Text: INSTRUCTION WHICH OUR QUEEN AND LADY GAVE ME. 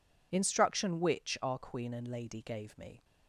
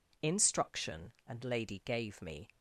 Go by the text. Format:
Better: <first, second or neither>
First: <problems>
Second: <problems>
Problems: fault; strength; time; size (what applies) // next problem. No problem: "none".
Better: first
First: none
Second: skips "WHICH OUR QUEEN"; at 1.2 s